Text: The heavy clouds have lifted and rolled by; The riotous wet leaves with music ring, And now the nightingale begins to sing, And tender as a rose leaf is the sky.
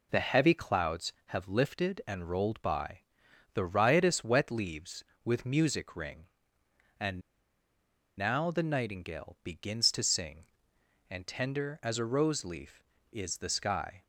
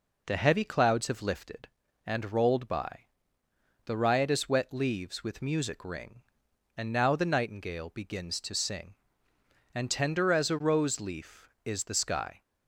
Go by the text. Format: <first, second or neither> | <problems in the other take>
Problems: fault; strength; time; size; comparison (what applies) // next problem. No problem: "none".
second | pauses between "And" and "now"; noticeable; at 7.2 s; 0.97 s long